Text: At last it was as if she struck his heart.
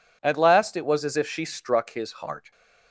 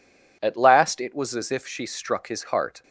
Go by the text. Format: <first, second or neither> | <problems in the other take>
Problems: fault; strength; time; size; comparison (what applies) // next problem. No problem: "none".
neither | none